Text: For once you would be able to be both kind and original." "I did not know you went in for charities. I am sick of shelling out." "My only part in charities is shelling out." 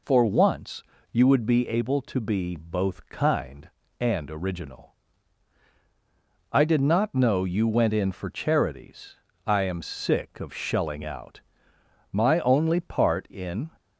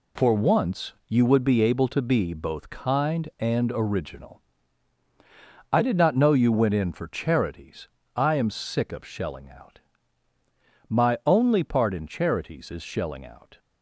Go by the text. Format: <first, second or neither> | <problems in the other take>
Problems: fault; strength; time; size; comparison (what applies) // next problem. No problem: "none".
second | pauses between "once" and "you"; slight; at 0.8 s; 0.30 s long // stops before "charities is shelling out"; at 13.7 s